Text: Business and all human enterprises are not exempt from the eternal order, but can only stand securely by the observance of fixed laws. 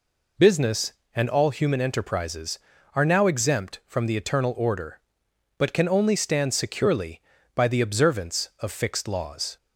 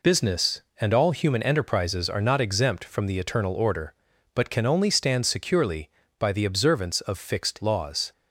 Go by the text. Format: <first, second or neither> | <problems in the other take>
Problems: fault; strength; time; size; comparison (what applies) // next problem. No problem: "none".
second | says "now" for "not"; at 3.0 s